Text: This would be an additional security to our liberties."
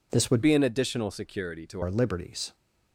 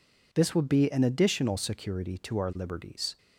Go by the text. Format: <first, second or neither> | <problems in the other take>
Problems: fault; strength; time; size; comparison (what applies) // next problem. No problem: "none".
second | changes voice from "be" to "to"; from 0.4 to 1.8 s; 1.4 s long